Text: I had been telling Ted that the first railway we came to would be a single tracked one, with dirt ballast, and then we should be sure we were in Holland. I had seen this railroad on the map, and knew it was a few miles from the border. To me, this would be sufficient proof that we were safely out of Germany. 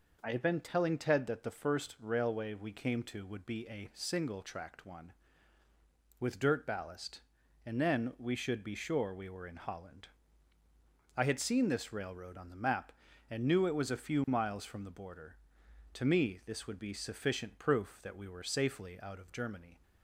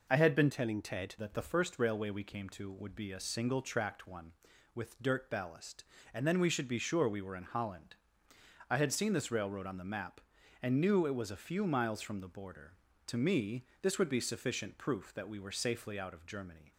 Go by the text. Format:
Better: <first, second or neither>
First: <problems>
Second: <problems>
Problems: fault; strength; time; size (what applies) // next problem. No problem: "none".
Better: first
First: none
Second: changes voice from "telling" to "Ted"; from 0.4 to 1.1 s; 0.7 s long